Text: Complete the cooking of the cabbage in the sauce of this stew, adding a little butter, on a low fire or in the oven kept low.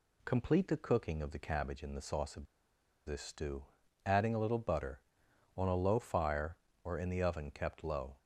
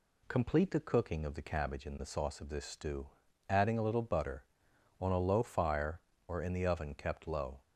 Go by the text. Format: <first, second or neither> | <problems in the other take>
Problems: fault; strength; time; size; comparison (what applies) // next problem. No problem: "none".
second | pauses between "of" and "this"; noticeable; at 2.4 s; 0.61 s long